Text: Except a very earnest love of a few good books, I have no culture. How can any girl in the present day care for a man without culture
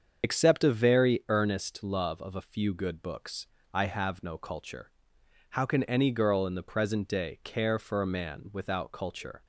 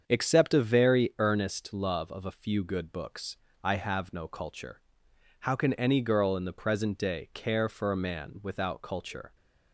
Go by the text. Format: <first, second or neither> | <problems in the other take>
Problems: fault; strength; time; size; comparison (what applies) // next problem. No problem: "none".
second | loses the start of "Except"; at 0.2 s; 70 ms // starts louder than the rest; until 1.2 s; 7 dB; strong in the second